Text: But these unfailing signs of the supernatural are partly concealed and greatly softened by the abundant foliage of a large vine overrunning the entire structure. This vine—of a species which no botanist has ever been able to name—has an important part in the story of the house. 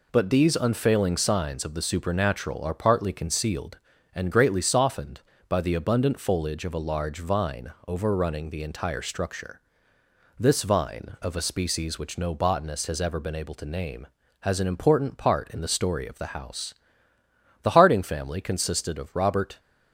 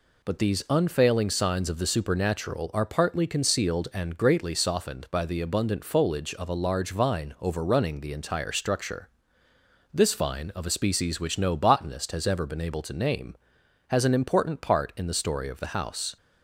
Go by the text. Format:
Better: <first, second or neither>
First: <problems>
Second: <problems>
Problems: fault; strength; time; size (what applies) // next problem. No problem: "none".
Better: second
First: pauses between "vine" and "overrunning"; slight; at 7.7 s; 0.16 s long // goes on to say "The Harding family consisted of Robert"; strong; from 17.6 s on; 1.9 s long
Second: none